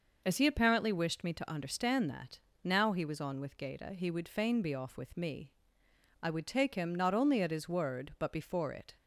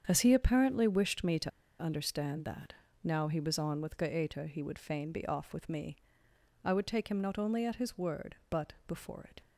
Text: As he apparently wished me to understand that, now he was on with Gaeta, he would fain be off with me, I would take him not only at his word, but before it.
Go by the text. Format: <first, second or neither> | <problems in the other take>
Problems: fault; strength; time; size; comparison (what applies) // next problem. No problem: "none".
first | starts louder than the rest; strong; until 1.0 s; 7.5 dB // pauses between "to" and "understand"; slight; at 1.5 s; 0.31 s long // pauses between "but" and "before"; slight; at 8.7 s; 0.16 s long